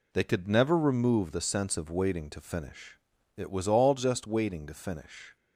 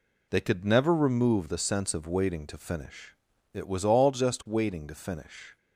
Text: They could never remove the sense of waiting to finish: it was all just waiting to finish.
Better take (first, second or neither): neither